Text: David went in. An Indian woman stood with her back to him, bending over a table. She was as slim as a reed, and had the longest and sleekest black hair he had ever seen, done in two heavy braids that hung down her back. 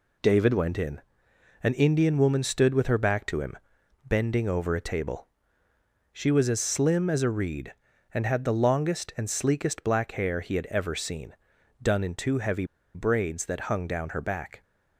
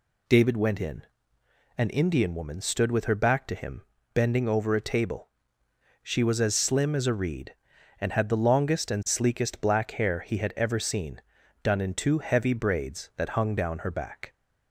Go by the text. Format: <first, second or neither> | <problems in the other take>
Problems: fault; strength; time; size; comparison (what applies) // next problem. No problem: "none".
second | pauses between "heavy" and "braids"; slight; at 12.6 s; 0.30 s long